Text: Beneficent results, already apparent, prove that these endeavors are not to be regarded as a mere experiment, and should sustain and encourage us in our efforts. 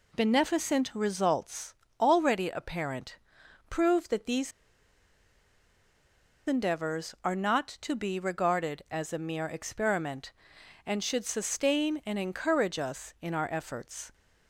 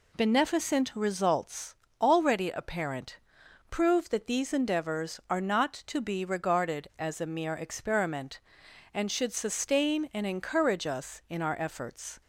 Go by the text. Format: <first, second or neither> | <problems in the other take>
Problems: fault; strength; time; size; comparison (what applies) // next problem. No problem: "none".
second | pauses between "these" and "endeavors"; strong; at 4.5 s; 1.9 s long